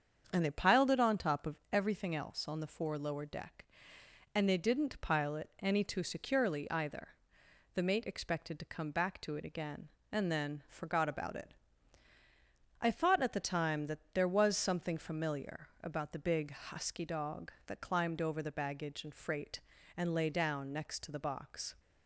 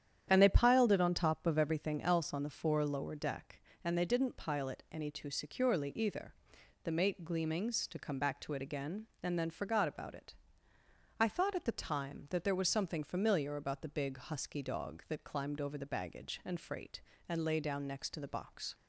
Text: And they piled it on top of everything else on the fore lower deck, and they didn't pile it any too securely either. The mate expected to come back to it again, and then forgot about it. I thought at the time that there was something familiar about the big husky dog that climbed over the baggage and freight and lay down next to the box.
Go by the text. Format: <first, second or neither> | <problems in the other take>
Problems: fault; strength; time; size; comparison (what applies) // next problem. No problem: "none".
first | starts louder than the rest; strong; until 1.2 s; 9.5 dB; strong in the first // says "gleamings" for "expected"; at 7.2 s